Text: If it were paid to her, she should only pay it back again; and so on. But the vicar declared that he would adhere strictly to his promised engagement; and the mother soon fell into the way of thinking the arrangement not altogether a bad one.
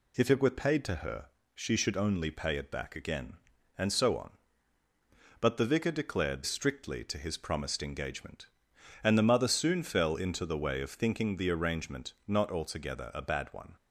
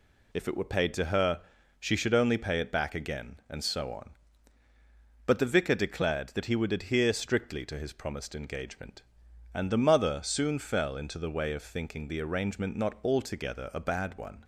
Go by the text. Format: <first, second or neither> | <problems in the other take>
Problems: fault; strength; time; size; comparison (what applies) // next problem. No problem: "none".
second | skips "that he would adhere"; at 6.4 s // pauses between "arrangement" and "not"; slight; at 12.1 s; 0.16 s long